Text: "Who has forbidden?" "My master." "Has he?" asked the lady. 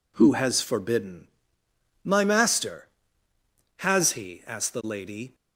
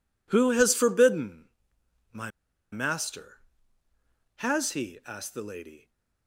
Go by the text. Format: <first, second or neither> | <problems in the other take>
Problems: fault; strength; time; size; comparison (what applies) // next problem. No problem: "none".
first | pauses between "My" and "master"; at 2.3 s; 0.41 s long